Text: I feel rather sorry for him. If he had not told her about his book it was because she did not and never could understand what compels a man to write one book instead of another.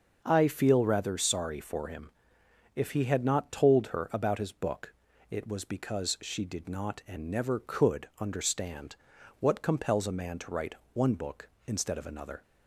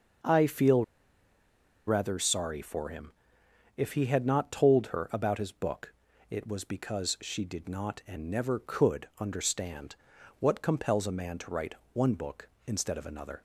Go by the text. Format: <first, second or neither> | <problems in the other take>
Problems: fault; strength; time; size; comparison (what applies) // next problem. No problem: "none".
first | starts louder than the rest; until 2.2 s; 6 dB; also in the first // pauses between "feel" and "rather"; at 0.8 s; 1.0 s long // pauses between "book" and "it"; slight; at 5.9 s; 0.36 s long; slight in the first // pauses between "understand" and "what"; at 9.9 s; 0.44 s long; also in the first // pauses between "write" and "one"; slight; at 11.7 s; 0.18 s long; slight in the first